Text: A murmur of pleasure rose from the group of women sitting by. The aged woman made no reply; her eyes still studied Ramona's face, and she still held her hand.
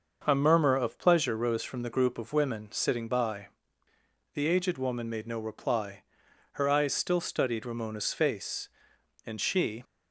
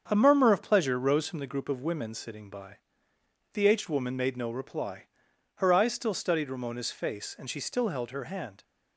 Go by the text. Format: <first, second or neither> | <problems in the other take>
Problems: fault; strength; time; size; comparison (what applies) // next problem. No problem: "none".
second | starts louder than the rest; until 1.2 s; 6.5 dB; strong in the second // stops before "still held her hand"; at 9.8 s